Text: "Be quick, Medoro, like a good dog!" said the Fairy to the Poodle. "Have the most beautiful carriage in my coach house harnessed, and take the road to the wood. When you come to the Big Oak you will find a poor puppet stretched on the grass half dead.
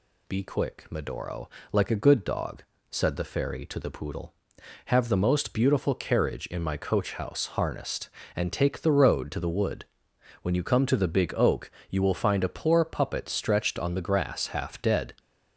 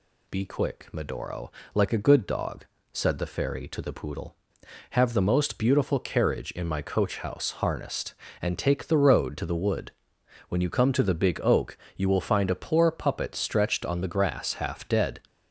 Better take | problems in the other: neither | pauses between "Oak" and "you"; slight; the same in both

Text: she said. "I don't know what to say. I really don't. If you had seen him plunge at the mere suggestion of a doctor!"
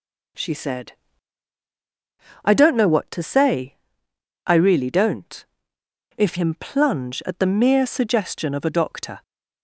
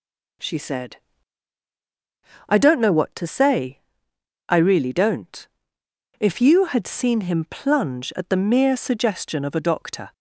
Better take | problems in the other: second | skips "you had seen"; at 6.3 s

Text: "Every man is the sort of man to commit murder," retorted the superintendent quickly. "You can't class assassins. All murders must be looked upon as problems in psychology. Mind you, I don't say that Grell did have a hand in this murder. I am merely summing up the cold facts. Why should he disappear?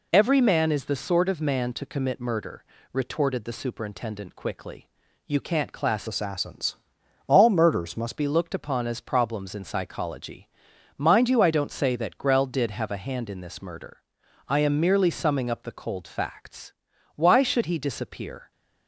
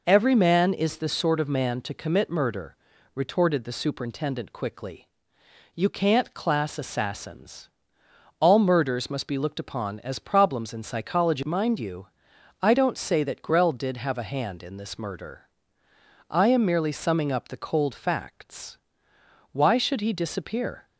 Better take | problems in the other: second | changes voice from "assassins" to "must"; from 6.0 to 8.1 s; 2.1 s long

